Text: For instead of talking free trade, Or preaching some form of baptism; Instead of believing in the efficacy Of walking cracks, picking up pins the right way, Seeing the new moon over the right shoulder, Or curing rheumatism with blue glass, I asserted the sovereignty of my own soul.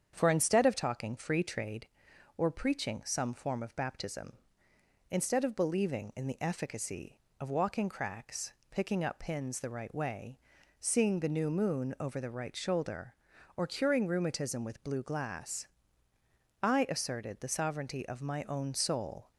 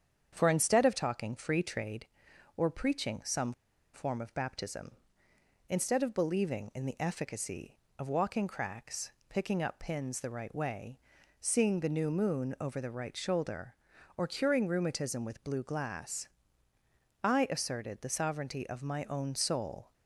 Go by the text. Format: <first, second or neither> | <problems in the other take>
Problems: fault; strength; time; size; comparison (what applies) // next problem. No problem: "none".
first | starts louder than the rest; strong; until 1.3 s; 8 dB; strong in the first // pauses between "some" and "form"; at 3.5 s; 0.41 s long